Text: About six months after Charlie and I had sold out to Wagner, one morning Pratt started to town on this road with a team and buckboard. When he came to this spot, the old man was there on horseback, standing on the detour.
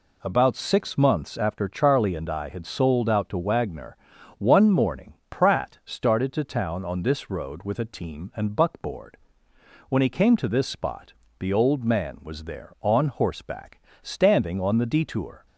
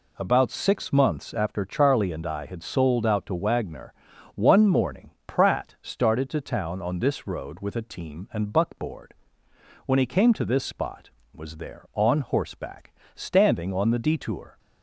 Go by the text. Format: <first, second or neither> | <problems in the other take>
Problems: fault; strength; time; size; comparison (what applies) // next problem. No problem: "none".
first | pauses between "morning" and "Pratt"; slight; at 5.1 s; 0.16 s long; slight in the first // skips "the old man"; at 11.2 s